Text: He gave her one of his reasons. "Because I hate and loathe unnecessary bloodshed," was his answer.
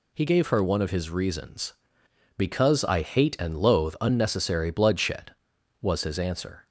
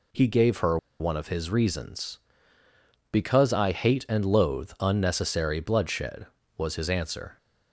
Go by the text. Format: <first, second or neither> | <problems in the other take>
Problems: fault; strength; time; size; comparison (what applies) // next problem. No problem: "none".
first | pauses between "her" and "one"; slight; at 0.7 s; 0.23 s long